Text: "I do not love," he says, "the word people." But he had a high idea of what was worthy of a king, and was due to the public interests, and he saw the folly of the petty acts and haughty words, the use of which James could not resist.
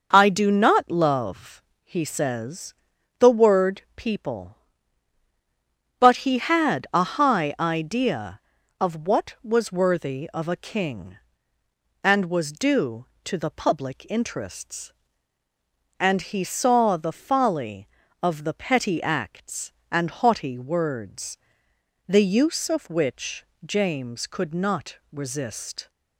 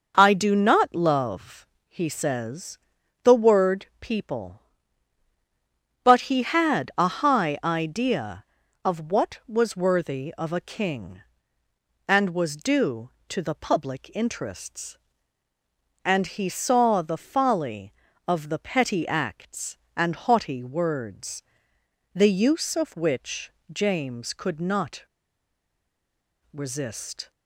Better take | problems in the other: first | pauses between "which" and "James"; slight; at 23.5 s; 0.18 s long; slight in the first // pauses between "not" and "resist"; strong; at 25.0 s; 1.4 s long

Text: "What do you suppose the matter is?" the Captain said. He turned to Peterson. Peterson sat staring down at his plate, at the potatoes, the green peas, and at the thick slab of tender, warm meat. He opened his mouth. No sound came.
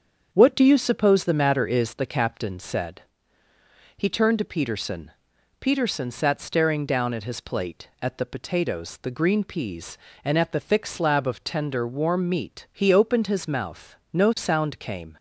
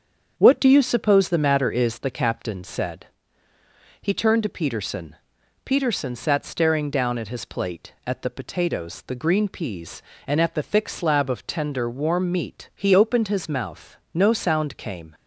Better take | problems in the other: neither | starts louder than the rest; strong; the same in both

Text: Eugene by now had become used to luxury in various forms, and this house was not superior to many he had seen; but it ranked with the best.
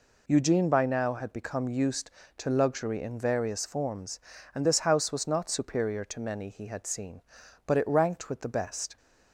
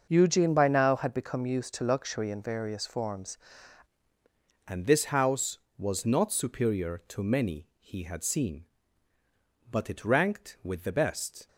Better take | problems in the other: first | starts louder than the rest; until 1.1 s; 6 dB // changes voice at "and"; from 4.6 s on; 6.8 s long

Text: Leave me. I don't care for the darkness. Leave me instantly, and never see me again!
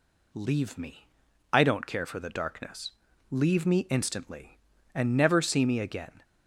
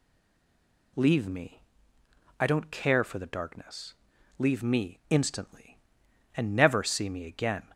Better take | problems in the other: first | stays silent before the first word; slight; until 0.9 s; 0.9 s long

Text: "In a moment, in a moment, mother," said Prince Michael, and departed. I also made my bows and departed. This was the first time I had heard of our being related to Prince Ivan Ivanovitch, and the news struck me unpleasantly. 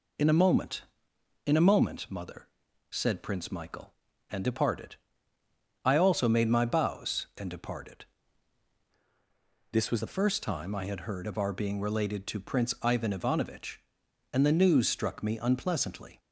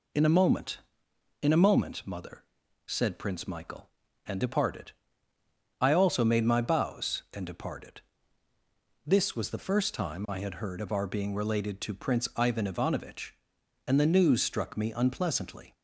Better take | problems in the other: second | changes voice from "This" to "was"; from 9.7 to 9.9 s; 0.2 s long

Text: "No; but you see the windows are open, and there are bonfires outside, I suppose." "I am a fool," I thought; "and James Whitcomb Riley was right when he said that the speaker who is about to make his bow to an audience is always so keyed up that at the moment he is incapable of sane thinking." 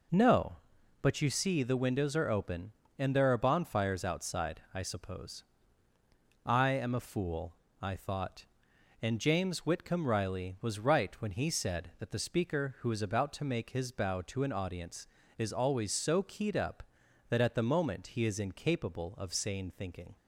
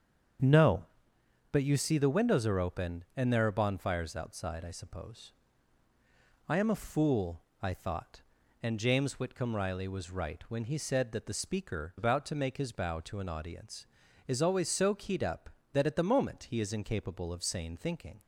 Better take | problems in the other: first | starts louder than the rest; strong; until 2.0 s; 7.5 dB // skips "who is"; at 11.9 s

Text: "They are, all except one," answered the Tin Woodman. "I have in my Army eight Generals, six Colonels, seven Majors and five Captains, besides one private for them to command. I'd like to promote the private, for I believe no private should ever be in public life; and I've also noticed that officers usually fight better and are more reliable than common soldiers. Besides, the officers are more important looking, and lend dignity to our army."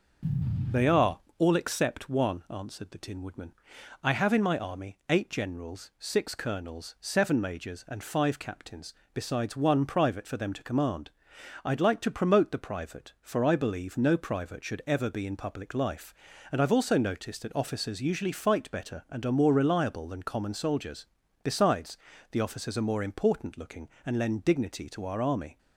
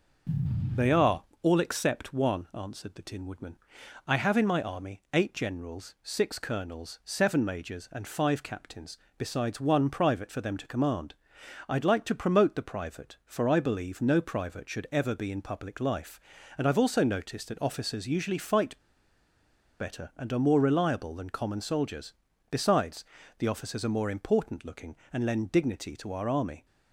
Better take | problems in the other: first | starts louder than the rest; until 1.9 s; 6.5 dB; also in the first // pauses between "fight" and "better"; at 18.7 s; 1.0 s long

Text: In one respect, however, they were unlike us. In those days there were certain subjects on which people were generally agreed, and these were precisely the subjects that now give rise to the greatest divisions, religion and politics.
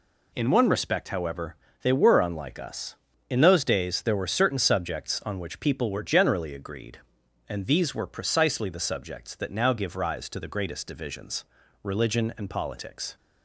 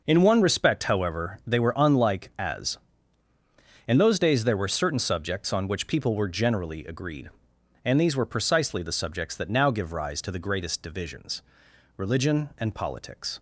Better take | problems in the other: first | says "as" for "us"; at 2.3 s

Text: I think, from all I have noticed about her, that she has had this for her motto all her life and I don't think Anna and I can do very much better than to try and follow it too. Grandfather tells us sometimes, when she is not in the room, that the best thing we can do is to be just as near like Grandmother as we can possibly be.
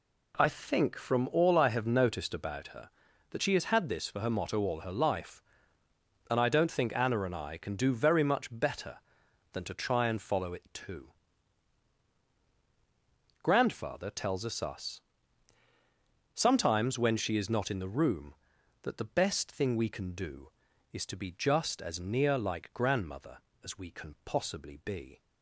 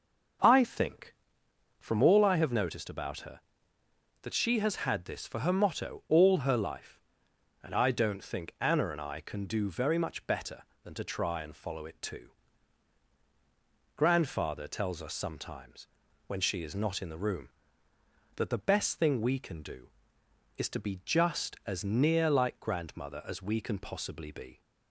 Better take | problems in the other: second | says "us" twice; at 14.5 s

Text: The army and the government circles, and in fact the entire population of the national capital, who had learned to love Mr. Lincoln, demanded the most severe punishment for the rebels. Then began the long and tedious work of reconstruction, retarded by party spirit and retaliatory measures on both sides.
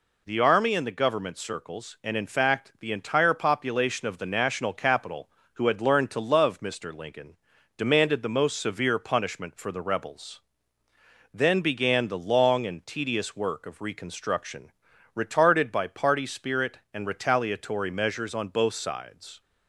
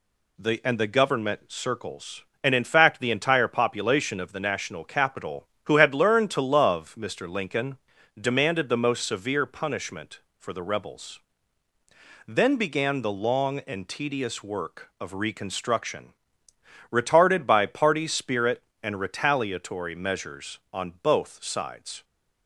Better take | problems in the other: first | skips "army"; at 0.6 s

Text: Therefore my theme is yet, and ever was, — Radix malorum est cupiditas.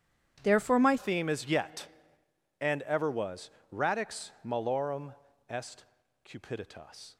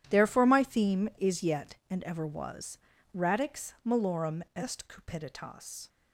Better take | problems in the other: second | changes voice at "theme"; from 0.9 s on; 6.2 s long // pauses between "malorum" and "est"; slight; at 5.1 s; 0.34 s long // pauses between "est" and "cupiditas"; at 5.8 s; 0.40 s long

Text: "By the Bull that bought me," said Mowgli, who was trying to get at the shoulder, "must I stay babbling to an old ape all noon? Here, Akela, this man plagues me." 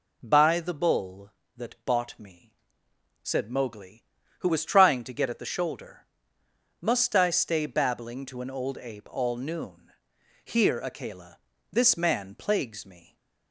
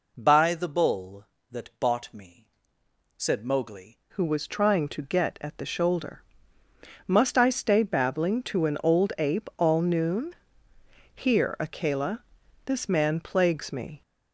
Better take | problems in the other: first | changes voice at "who"; from 4.1 s on; 9.9 s long

